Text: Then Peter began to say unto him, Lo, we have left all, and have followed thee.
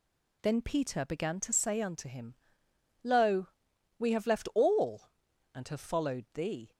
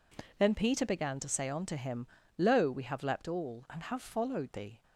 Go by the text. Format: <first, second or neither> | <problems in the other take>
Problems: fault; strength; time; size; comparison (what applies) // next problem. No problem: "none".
first | says "leapt" for "left"; at 3.0 s